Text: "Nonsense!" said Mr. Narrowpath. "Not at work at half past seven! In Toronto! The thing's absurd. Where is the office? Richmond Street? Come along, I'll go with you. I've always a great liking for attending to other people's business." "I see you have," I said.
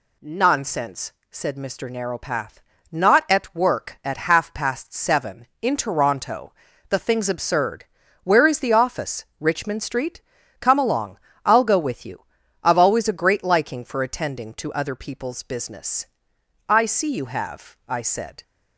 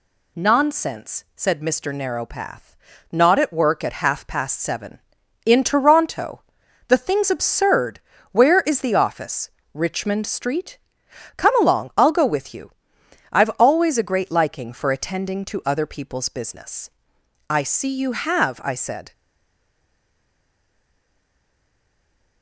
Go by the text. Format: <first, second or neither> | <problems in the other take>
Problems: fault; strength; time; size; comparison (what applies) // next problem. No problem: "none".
first | stays silent after the last word; strong; from 19.1 s on; 3.3 s long